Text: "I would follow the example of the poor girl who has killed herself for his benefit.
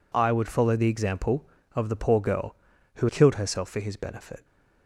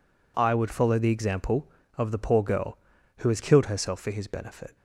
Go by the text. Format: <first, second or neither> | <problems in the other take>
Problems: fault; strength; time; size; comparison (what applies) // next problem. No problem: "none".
second | skips "has"; at 3.0 s